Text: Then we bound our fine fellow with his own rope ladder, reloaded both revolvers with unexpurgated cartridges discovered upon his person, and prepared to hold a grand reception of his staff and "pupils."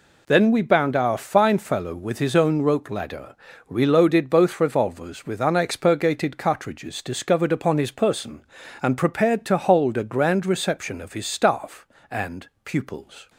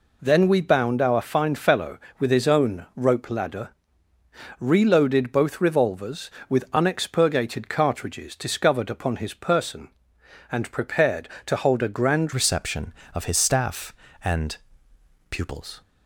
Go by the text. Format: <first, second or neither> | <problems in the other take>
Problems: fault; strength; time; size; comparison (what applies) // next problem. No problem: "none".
first | changes voice at "reception"; from 12.3 s on; 3.5 s long // pauses between "and" and "pupils"; noticeable; at 14.5 s; 0.74 s long; slight in the first